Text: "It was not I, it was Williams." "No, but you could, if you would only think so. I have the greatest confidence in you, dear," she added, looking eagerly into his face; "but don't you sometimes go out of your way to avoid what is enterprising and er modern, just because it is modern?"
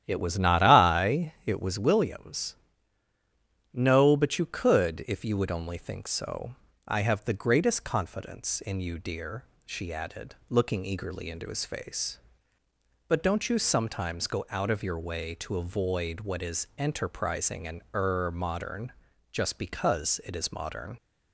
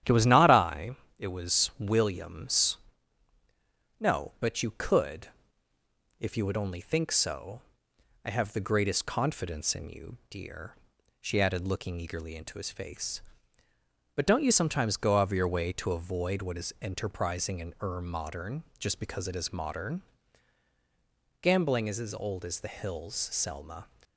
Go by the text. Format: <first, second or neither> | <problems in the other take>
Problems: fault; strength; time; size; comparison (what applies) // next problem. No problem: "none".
first | starts louder than the rest; strong; until 1.2 s; 10.5 dB; strong in the first // goes on to say "Gambling is as old as the hills Selma"; strong; from 21.4 s on; 2.4 s long